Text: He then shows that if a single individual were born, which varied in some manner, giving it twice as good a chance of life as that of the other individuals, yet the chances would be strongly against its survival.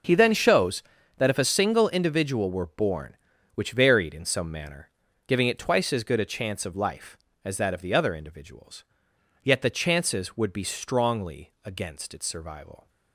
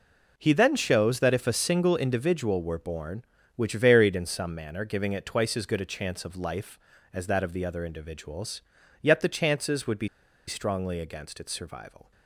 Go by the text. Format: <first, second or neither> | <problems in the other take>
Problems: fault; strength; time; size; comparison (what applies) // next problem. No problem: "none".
first | pauses between "be" and "strongly"; at 10.0 s; 0.40 s long